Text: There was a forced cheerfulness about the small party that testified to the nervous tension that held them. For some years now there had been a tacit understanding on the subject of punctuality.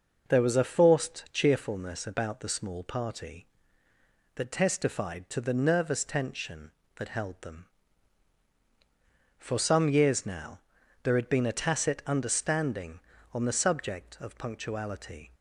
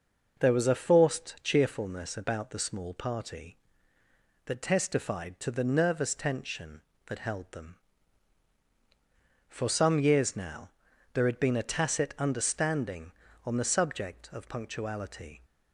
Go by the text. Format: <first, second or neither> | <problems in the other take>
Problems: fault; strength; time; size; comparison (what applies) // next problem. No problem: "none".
neither | pauses between "now" and "there"; the same in both